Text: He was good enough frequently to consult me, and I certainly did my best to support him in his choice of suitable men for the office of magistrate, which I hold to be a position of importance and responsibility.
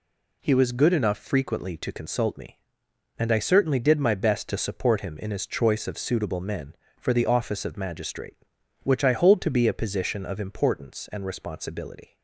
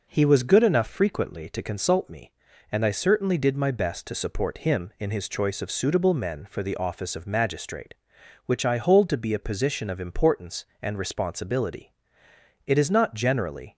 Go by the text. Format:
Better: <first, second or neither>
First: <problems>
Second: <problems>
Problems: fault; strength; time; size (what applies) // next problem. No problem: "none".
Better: first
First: none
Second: goes on to say "It is not generally"; noticeable; from 12.6 s on; 1.1 s long